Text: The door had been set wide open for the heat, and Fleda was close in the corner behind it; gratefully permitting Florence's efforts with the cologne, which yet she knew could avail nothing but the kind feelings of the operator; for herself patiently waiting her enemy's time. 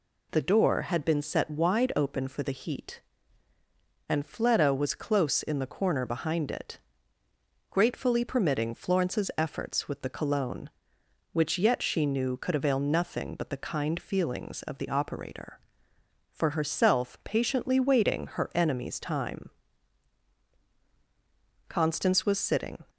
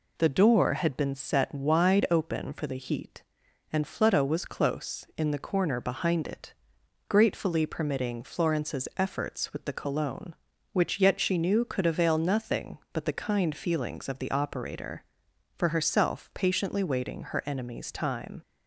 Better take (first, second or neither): second